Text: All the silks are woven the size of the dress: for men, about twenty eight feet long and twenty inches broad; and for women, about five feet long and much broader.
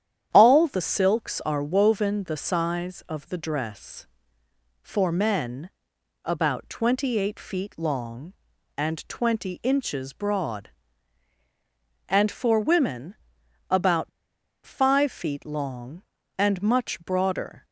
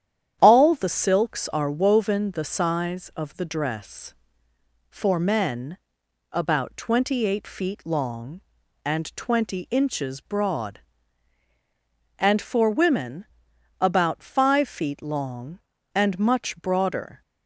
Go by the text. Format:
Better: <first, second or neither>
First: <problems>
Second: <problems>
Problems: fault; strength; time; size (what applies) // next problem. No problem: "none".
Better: second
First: starts louder than the rest; strong; until 1.3 s; 10 dB // pauses between "about" and "five"; noticeable; at 14.0 s; 0.56 s long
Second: starts louder than the rest; strong; until 1.4 s; 10 dB